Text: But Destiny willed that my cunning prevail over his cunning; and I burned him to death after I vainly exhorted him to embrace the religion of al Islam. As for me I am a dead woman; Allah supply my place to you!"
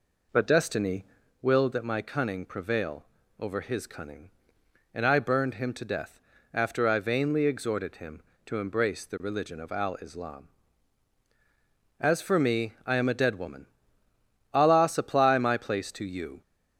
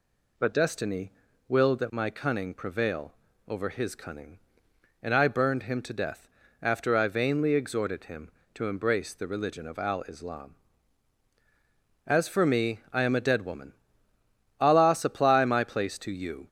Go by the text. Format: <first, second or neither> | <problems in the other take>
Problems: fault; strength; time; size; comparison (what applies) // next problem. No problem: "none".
second | starts louder than the rest; noticeable; until 1.3 s; 4 dB // pauses between "Destiny" and "willed"; slight; at 1.0 s; 0.36 s long; slight in the second // pauses between "prevail" and "over"; slight; at 3.0 s; 0.34 s long; slight in the second // pauses between "death" and "after"; slight; at 6.1 s; 0.34 s long; slight in the second